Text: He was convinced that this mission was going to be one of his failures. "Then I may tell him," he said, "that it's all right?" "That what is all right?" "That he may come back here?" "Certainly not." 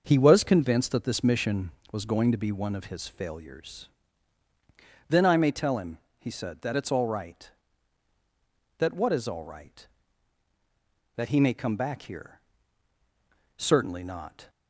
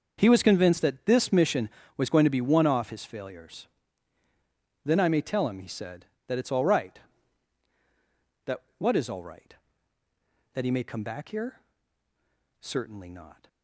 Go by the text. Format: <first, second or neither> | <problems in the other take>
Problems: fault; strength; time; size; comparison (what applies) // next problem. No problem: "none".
first | starts louder than the rest; until 1.2 s; 6.5 dB; also in the first // says "off" for "of"; at 2.6 s // pauses between "That" and "what"; slight; at 8.6 s; 0.16 s long